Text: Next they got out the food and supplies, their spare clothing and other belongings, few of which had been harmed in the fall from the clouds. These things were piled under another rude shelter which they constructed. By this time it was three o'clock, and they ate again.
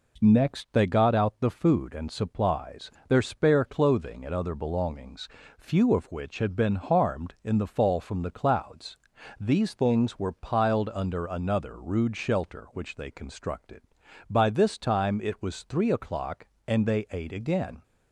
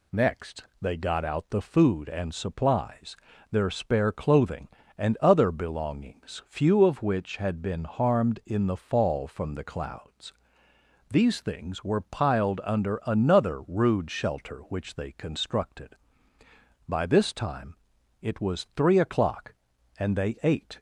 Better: first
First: none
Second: pauses between "Next" and "they"; slight; at 0.6 s; 0.18 s long // pauses between "time" and "it"; noticeable; at 17.7 s; 0.46 s long // stops before "again"; at 20.7 s

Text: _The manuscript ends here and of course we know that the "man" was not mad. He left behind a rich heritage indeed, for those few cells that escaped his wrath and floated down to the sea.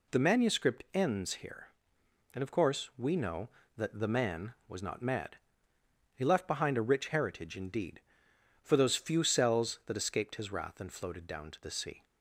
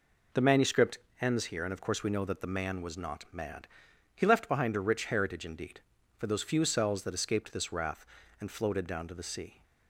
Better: first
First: none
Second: pauses between "manuscript" and "ends"; slight; at 0.9 s; 0.22 s long // says "this" for "his"; at 7.5 s

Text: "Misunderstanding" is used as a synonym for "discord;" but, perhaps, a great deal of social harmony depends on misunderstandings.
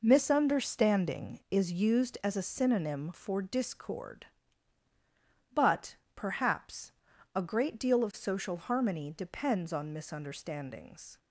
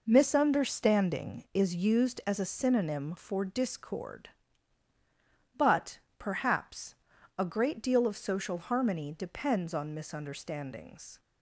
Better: neither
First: none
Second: none

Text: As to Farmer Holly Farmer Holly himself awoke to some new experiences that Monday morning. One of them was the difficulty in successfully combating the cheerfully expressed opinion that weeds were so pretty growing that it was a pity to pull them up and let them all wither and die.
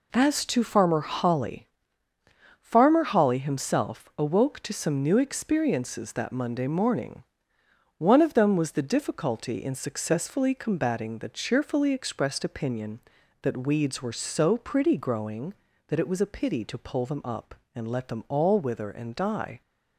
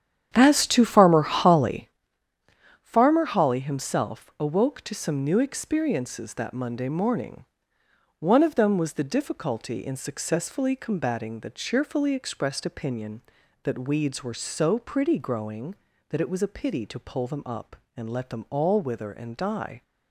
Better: first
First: pauses between "Holly" and "Farmer"; noticeable; at 1.6 s; 0.90 s long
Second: starts louder than the rest; strong; until 2.0 s; 9.5 dB // pauses between "Holly" and "Farmer"; noticeable; at 1.9 s; 0.90 s long

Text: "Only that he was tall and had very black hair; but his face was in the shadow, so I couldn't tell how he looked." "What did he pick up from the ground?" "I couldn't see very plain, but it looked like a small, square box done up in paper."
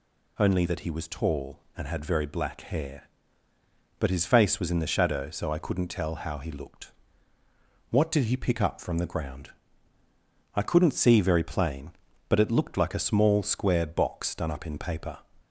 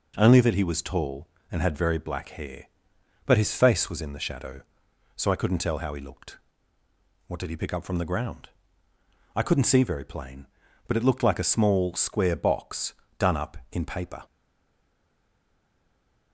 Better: first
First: none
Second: pauses between "box" and "done"; slight; at 12.9 s; 0.24 s long // stays silent after the last word; noticeable; from 14.2 s on; 2.1 s long

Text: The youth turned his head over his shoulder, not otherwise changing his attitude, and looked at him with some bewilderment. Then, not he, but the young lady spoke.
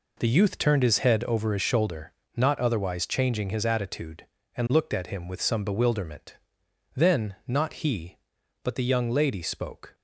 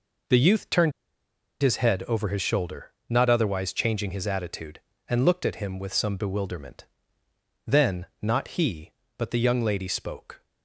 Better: first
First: none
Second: pauses between "turned" and "his"; noticeable; at 0.9 s; 0.70 s long

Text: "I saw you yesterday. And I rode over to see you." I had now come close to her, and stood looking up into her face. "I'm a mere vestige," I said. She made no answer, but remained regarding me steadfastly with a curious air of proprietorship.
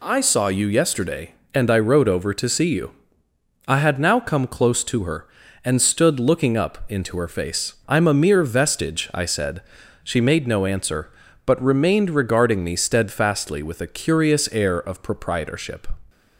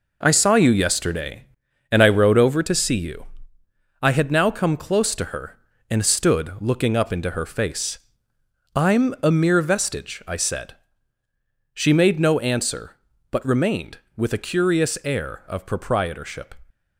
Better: first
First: none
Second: skips "regarding me steadfastly"; at 14.0 s

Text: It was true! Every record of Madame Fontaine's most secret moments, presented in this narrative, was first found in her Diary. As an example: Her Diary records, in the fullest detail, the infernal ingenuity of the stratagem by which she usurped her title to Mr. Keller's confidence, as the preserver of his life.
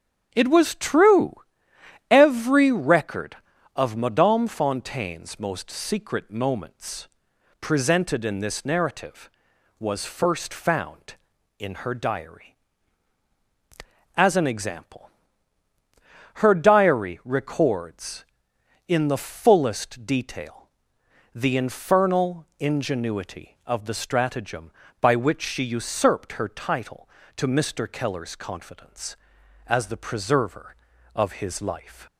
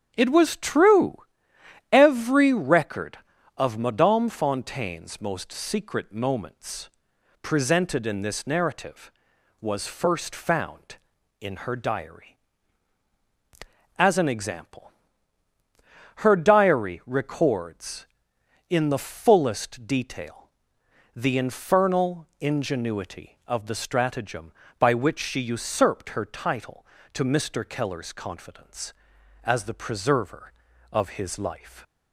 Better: neither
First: starts louder than the rest; strong; until 1.3 s; 8.5 dB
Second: starts louder than the rest; strong; until 1.1 s; 8.5 dB

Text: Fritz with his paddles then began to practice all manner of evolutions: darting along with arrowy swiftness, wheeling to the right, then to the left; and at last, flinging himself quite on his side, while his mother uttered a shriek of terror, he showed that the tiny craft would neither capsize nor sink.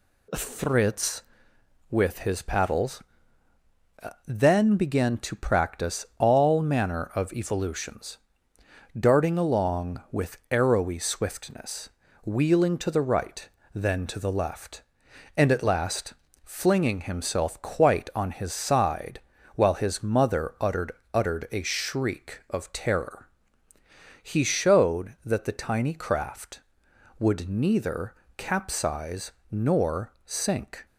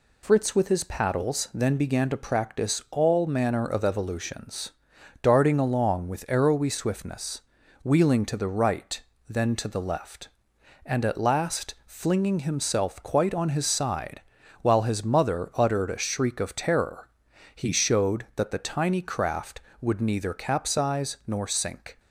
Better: second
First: pauses between "paddles" and "then"; at 3.0 s; 1.2 s long // says "uttered" twice; at 21.1 s // pauses between "neither" and "capsize"; slight; at 28.1 s; 0.24 s long // pauses between "capsize" and "nor"; slight; at 29.3 s; 0.20 s long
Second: none

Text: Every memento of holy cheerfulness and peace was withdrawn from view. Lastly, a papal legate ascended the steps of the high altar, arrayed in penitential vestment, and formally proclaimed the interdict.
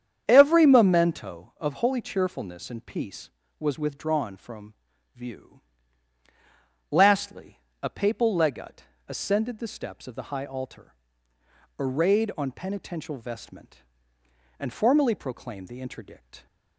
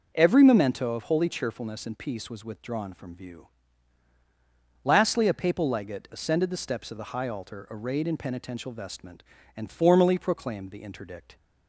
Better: second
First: starts louder than the rest; strong; until 1.2 s; 8.5 dB // pauses between "from" and "view"; at 4.7 s; 0.40 s long // pauses between "legate" and "ascended"; slight; at 8.8 s; 0.26 s long // says "on" for "in"; at 12.3 s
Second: none

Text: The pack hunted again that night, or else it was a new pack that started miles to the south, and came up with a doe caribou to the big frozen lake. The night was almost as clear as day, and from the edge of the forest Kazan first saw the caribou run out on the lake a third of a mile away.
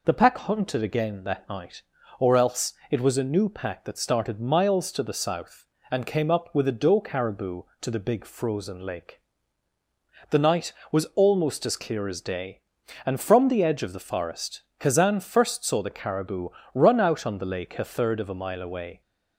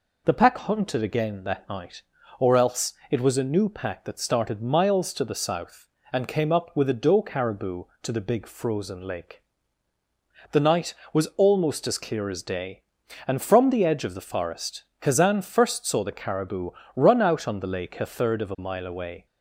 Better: neither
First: pauses between "else" and "it"; slight; at 2.7 s; 0.18 s long // pauses between "forest" and "Kazan"; slight; at 14.6 s; 0.16 s long // pauses between "caribou" and "run"; slight; at 16.4 s; 0.24 s long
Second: pauses between "else" and "it"; slight; at 2.9 s; 0.18 s long // pauses between "forest" and "Kazan"; slight; at 14.8 s; 0.16 s long // pauses between "caribou" and "run"; slight; at 16.7 s; 0.24 s long

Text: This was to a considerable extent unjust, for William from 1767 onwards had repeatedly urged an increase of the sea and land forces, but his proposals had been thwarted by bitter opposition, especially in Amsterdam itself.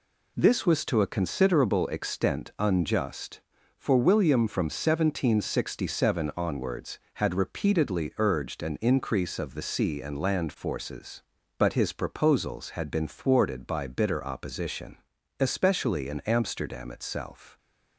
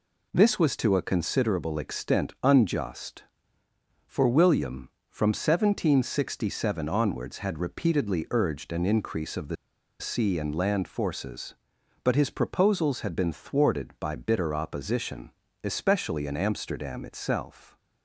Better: first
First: none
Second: pauses between "the" and "sea"; at 9.5 s; 0.44 s long

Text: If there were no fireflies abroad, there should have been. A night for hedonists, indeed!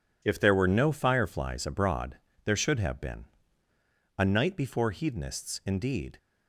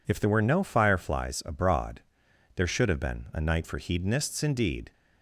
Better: second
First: says "before" for "for"; at 4.5 s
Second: none

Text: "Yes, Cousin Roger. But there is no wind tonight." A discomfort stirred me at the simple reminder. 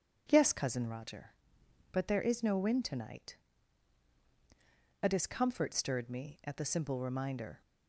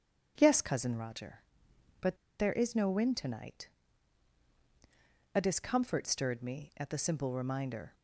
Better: first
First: none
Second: starts louder than the rest; strong; until 1.3 s; 7.5 dB // pauses between "But" and "there"; slight; at 2.1 s; 0.23 s long

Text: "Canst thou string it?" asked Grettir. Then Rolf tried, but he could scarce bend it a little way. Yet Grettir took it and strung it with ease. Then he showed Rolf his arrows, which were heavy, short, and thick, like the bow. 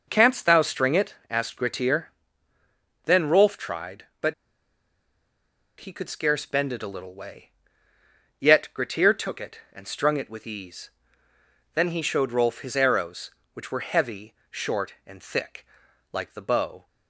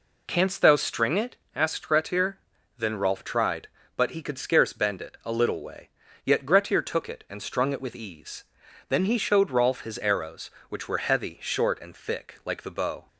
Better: second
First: pauses between "but" and "he"; strong; at 4.3 s; 1.4 s long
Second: none

